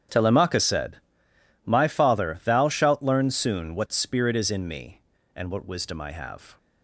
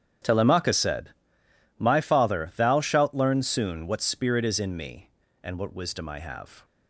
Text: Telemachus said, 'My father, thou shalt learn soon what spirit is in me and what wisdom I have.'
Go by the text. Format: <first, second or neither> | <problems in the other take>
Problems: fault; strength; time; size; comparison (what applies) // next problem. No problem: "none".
neither | starts louder than the rest; strong; the same in both